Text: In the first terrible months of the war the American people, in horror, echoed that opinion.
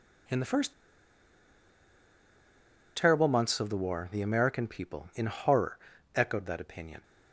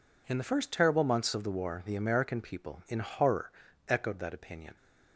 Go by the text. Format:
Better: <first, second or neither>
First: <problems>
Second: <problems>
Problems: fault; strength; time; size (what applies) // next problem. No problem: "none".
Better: second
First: pauses between "first" and "terrible"; strong; at 0.7 s; 2.2 s long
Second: none